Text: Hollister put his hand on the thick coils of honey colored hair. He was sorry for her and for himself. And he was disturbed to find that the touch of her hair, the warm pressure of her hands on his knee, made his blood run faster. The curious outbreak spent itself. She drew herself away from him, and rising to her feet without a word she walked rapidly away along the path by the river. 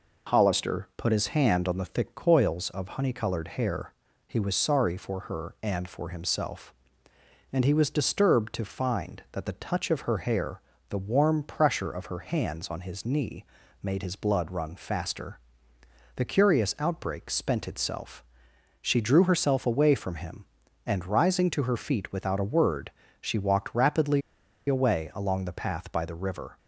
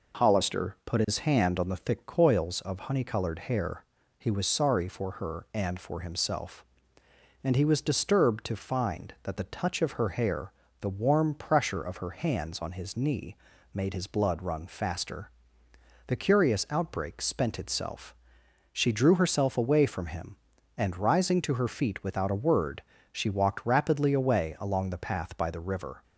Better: second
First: pauses between "word" and "she"; slight; at 22.8 s; 0.32 s long // pauses between "rapidly" and "away"; noticeable; at 24.2 s; 0.46 s long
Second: pauses between "word" and "she"; slight; at 22.8 s; 0.32 s long

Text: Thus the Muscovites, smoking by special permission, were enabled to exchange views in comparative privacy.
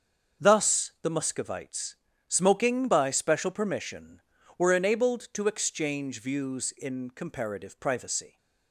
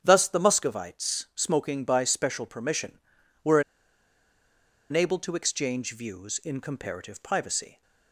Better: first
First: starts louder than the rest; until 1.4 s; 6.5 dB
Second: starts louder than the rest; strong; until 1.0 s; 8 dB // pauses between "were" and "enabled"; strong; at 3.6 s; 1.2 s long

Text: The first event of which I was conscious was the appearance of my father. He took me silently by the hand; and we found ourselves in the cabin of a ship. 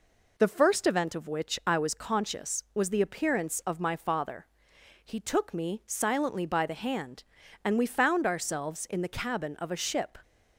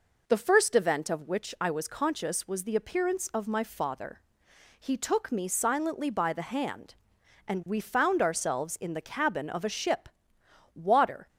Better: first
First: none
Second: goes on to say "Water"; from 10.7 s on; 0.54 s long

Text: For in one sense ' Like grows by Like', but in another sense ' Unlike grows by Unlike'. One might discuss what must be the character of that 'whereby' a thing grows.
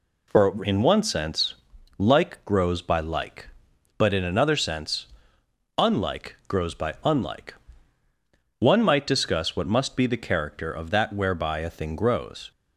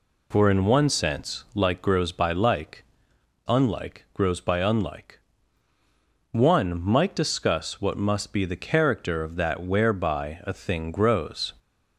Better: first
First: none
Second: skips "but in another sense"; at 3.1 s

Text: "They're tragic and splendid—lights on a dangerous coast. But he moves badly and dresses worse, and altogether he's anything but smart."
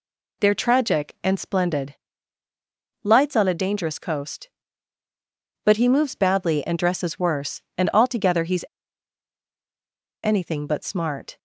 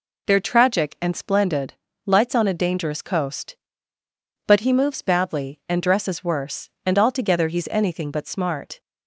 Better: second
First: pauses between "he's" and "anything"; strong; at 8.6 s; 1.5 s long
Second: none

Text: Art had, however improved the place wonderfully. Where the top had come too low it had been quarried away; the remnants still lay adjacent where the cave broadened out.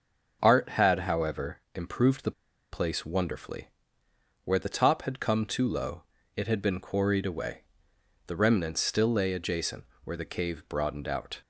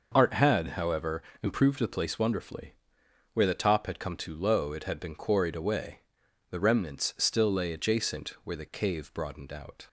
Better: second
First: starts louder than the rest; until 1.4 s; 6.5 dB // pauses between "however" and "improved"; slight; at 1.5 s; 0.16 s long // pauses between "the" and "place"; at 2.3 s; 0.40 s long // pauses between "low" and "it"; slight; at 6.0 s; 0.34 s long // pauses between "adjacent" and "where"; slight; at 9.8 s; 0.20 s long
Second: starts louder than the rest; noticeable; until 1.1 s; 6 dB // pauses between "however" and "improved"; slight; at 1.2 s; 0.18 s long

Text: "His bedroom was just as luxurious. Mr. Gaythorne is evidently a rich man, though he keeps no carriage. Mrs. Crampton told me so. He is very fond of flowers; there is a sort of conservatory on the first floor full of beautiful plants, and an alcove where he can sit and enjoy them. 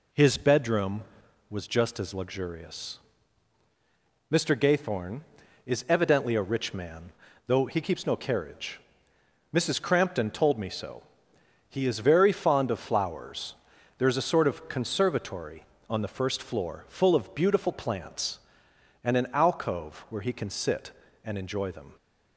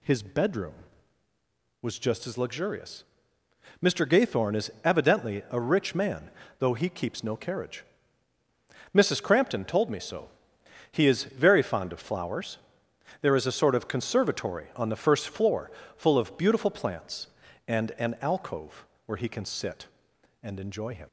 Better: first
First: none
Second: pauses between "floor" and "full"; slight; at 15.7 s; 0.24 s long // pauses between "alcove" and "where"; slight; at 18.8 s; 0.20 s long // says "him" for "them"; at 20.9 s

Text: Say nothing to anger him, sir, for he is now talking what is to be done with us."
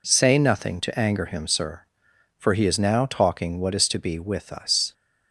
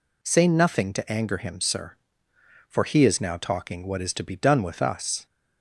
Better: second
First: skips "done"; at 4.1 s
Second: none

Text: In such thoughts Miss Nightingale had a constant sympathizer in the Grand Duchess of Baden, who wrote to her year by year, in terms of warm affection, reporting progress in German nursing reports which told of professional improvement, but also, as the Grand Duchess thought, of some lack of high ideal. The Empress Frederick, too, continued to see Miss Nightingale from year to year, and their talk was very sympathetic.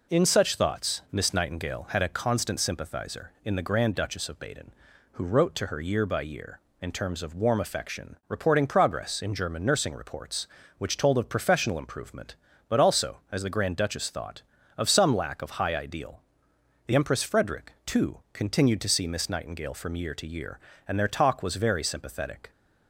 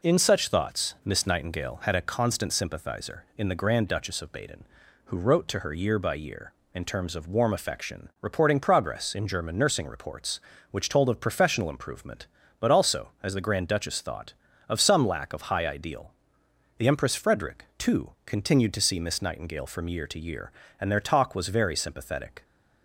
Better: neither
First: none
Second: none

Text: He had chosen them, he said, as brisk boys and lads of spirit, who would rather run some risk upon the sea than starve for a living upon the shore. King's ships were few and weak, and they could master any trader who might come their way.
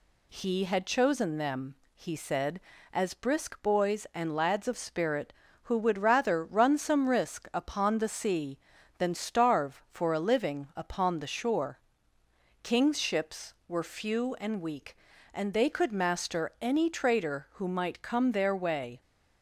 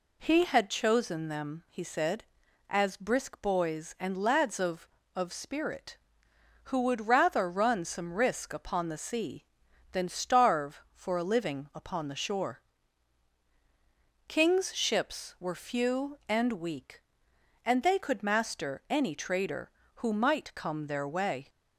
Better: first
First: none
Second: says "of" twice; at 5.1 s

